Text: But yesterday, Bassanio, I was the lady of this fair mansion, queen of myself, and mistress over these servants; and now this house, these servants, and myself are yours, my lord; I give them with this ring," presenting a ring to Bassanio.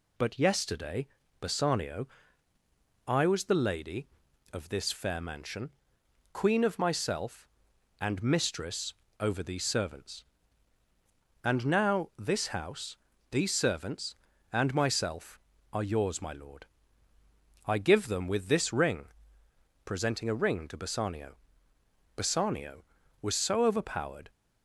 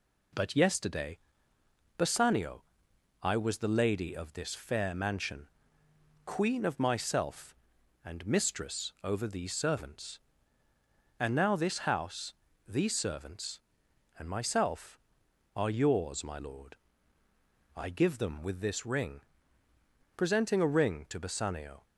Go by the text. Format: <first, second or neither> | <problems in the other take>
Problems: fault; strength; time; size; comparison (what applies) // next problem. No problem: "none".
second | pauses between "mistress" and "over"; slight; at 8.9 s; 0.26 s long // goes on to say "Bassanio was so overpowered"; strong; from 22.1 s on; 2.1 s long